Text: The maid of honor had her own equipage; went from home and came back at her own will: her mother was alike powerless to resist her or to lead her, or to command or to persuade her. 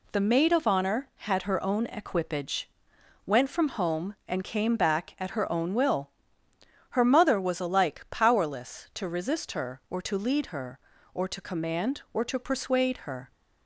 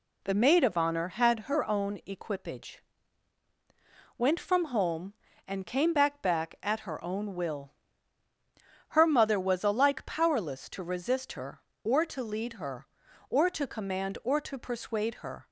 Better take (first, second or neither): first